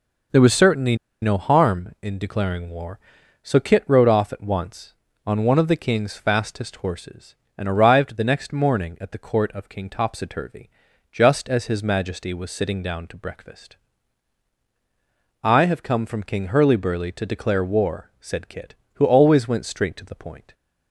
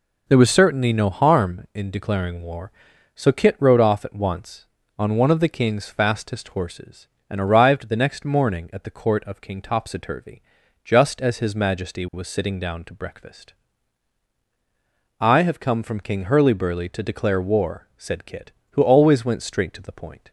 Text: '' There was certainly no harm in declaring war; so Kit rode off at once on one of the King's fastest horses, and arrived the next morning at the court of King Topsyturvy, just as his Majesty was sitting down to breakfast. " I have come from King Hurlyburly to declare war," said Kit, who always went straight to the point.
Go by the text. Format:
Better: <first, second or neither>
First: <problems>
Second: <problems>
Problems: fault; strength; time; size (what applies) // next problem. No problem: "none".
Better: second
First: pauses between "certainly" and "no"; slight; at 0.9 s; 0.27 s long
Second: none